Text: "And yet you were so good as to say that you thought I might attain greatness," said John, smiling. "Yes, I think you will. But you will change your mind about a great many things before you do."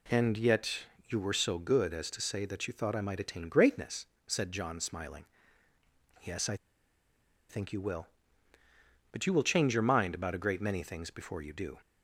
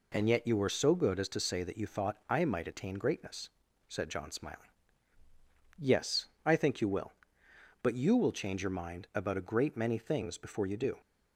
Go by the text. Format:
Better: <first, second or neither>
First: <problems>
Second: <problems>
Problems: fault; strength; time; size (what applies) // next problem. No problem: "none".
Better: second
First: pauses between "yet" and "you"; slight; at 0.8 s; 0.24 s long // pauses between "I" and "think"; noticeable; at 6.5 s; 0.94 s long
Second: none